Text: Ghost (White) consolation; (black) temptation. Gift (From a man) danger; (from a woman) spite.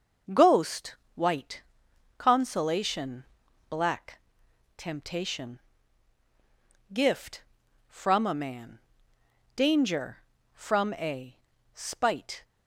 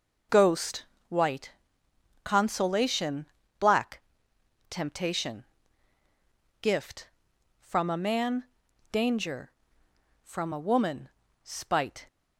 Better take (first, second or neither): second